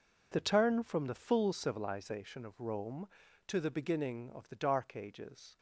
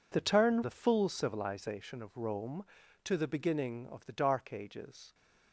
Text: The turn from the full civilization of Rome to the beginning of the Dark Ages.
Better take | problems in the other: first | skips "from"; at 0.6 s

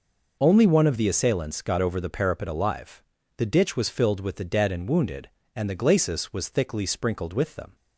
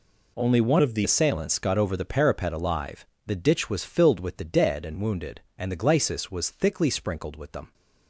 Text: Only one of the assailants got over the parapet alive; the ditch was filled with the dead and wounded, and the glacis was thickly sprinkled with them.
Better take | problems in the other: first | changes voice from "of" to "the"; from 0.8 to 1.0 s; 0.2 s long

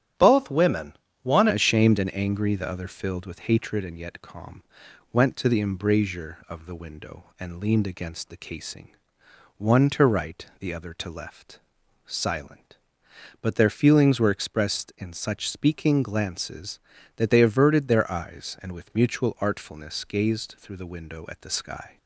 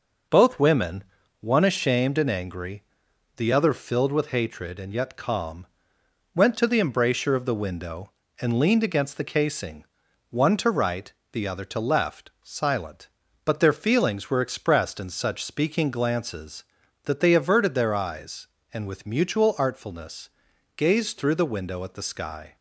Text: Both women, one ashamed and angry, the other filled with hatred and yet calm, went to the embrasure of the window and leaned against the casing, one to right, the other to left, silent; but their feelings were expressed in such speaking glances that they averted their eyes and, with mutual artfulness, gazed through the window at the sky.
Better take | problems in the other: second | starts louder than the rest; strong; until 1.4 s; 10 dB // changes voice at "ashamed"; from 1.5 s on; 20.4 s long

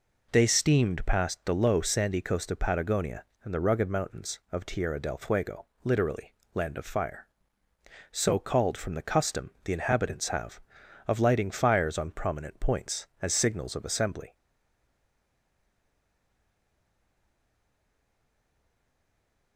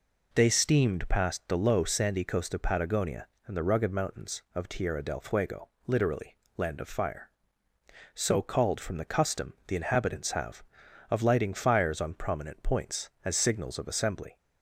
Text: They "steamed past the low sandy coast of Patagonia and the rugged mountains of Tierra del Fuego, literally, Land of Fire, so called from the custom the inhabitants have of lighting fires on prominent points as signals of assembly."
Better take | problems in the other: second | stays silent after the last word; strong; from 14.3 s on; 5.2 s long

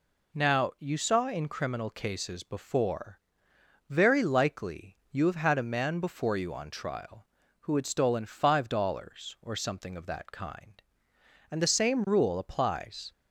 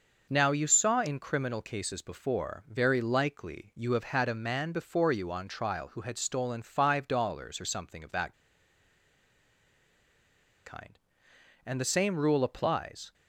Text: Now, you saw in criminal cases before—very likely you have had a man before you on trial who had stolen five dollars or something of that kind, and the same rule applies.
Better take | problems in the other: first | pauses between "that" and "kind"; strong; at 8.3 s; 2.3 s long

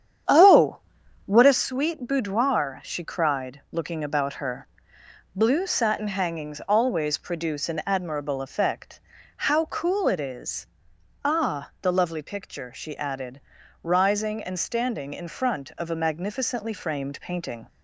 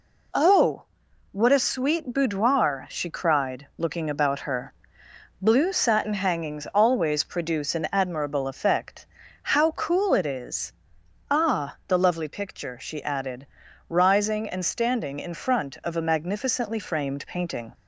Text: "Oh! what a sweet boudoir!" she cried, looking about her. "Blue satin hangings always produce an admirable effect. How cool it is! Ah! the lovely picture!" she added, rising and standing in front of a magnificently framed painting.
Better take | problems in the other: second | starts louder than the rest; strong; until 1.7 s; 9 dB

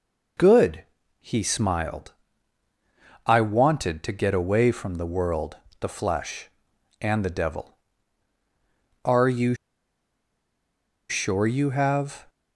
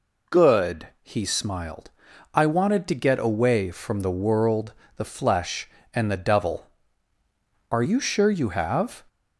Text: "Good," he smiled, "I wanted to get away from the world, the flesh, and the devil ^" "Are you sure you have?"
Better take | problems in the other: second | pauses between "you" and "sure"; strong; at 9.5 s; 1.5 s long

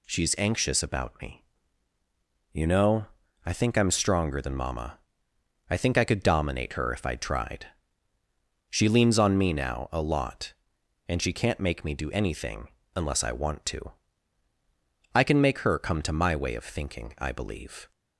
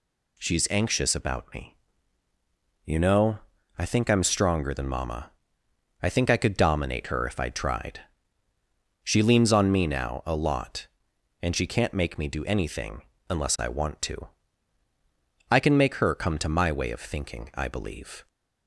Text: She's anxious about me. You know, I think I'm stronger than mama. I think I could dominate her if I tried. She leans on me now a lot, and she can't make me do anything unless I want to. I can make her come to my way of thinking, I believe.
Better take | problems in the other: neither | pauses between "anything" and "unless"; slight; the same in both

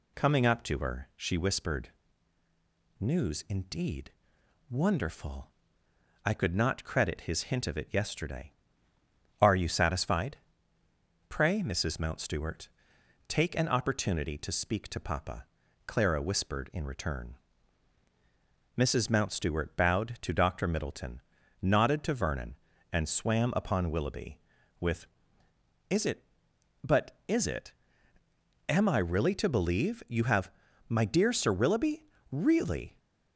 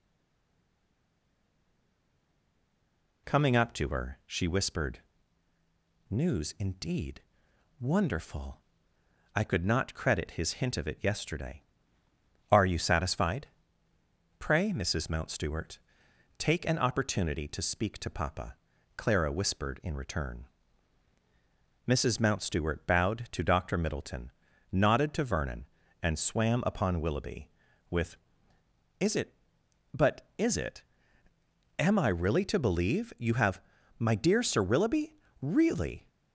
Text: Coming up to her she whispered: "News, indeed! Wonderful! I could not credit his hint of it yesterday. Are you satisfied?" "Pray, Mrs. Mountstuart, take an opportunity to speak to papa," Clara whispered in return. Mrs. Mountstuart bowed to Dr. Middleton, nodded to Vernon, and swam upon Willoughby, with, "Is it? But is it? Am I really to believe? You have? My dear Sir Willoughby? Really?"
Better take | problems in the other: first | stays silent before the first word; strong; until 3.2 s; 3.2 s long

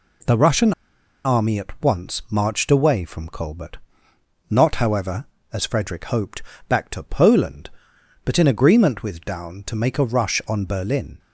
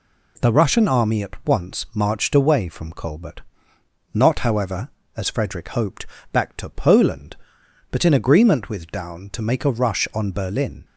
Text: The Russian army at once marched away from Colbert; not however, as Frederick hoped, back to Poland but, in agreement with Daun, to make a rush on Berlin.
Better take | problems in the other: second | pauses between "Russian" and "army"; noticeable; at 0.7 s; 0.53 s long

